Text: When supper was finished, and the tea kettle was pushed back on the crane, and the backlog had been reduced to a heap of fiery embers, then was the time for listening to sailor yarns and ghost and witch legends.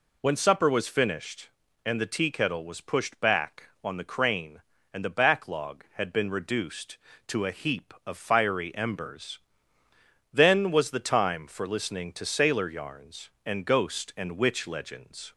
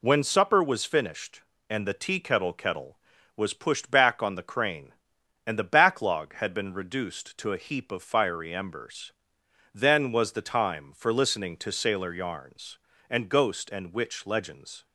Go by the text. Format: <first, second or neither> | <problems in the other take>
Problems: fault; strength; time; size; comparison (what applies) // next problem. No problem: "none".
first | says "kettle" twice; at 2.5 s